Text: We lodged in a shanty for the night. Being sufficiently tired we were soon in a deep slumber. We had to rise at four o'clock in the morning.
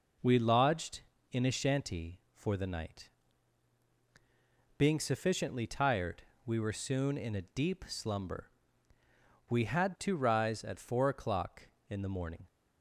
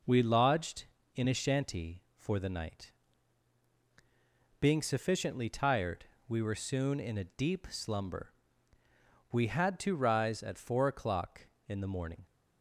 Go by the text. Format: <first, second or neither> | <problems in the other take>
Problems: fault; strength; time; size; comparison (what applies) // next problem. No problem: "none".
neither | pauses between "tired" and "we"; slight; the same in both